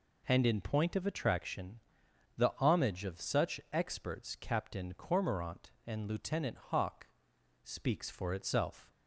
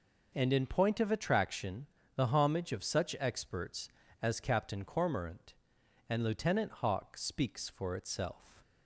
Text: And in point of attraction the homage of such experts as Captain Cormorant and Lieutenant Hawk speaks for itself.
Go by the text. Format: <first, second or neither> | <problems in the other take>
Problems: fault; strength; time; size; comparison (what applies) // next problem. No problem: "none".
second | pauses between "attraction" and "the"; noticeable; at 1.7 s; 0.58 s long; slight in the second // skips "as"; at 4.3 s // pauses between "Hawk" and "speaks"; noticeable; at 7.0 s; 0.56 s long